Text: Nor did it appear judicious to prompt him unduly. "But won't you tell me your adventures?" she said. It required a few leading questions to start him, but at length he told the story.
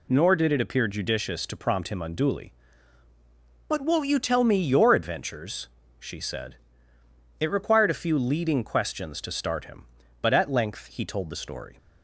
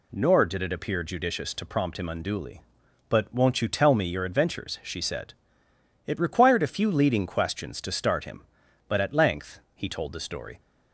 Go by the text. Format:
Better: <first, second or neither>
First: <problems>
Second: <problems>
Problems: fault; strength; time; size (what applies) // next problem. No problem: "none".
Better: neither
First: none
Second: none